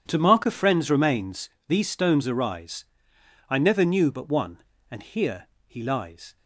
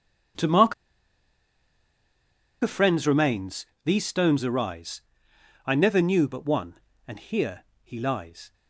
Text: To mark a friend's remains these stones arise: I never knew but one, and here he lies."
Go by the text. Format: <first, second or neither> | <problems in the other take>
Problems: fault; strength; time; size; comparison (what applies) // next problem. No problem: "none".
first | pauses between "mark" and "a"; strong; at 0.7 s; 1.8 s long // pauses between "remains" and "these"; slight; at 3.6 s; 0.18 s long; slight in the first // pauses between "here" and "he"; slight; at 7.6 s; 0.18 s long; slight in the first